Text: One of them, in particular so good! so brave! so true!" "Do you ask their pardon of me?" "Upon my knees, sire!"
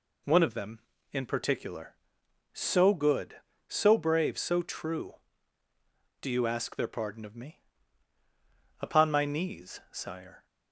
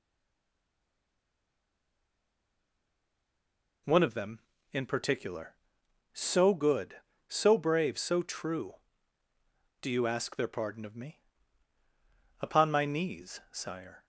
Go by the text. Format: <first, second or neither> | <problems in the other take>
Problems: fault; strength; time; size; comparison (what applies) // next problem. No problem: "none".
first | stays silent before the first word; strong; until 3.8 s; 3.8 s long